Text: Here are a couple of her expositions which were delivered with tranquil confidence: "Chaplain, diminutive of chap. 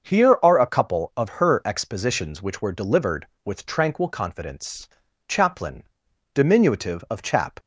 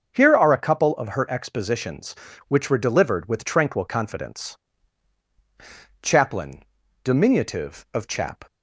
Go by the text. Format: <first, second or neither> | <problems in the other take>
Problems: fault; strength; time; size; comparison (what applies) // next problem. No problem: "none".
neither | starts louder than the rest; the same in both